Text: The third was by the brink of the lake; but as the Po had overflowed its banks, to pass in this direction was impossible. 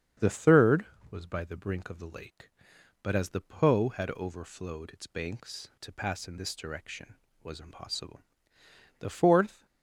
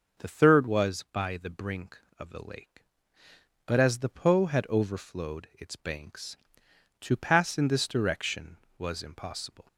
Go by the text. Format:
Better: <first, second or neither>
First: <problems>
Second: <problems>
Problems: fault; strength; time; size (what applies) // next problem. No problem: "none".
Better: second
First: starts louder than the rest; strong; until 1.4 s; 7.5 dB // goes on to say "The fourth"; noticeable; from 8.9 s on; 0.66 s long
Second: starts louder than the rest; until 1.2 s; 6.5 dB